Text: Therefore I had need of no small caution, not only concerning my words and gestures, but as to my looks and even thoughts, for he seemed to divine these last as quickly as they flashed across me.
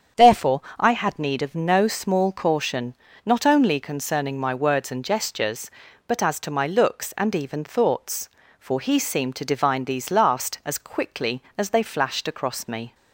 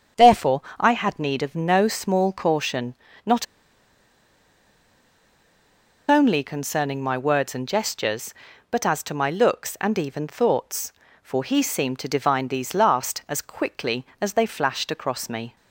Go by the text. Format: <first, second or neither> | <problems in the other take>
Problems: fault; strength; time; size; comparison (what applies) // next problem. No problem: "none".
first | starts louder than the rest; strong; until 1.3 s; 8 dB; strong in the first // pauses between "Therefore" and "I"; slight; at 0.6 s; 0.18 s long; slight in the first // pauses between "not" and "only"; strong; at 3.4 s; 2.6 s long